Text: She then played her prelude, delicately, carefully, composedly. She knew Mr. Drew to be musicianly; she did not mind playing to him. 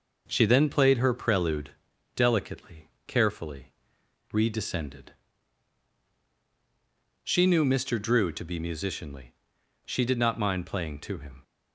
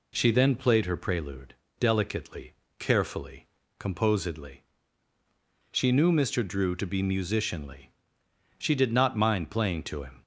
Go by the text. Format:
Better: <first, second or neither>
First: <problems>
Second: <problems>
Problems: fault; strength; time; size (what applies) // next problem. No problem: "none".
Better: second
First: says "redescended" for "composedly"; at 4.3 s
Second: none